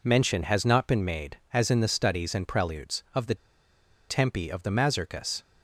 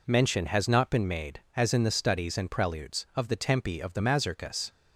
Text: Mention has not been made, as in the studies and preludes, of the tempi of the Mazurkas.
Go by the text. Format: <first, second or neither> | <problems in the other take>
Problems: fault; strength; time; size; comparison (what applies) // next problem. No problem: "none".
second | pauses between "the" and "tempi"; noticeable; at 3.3 s; 0.73 s long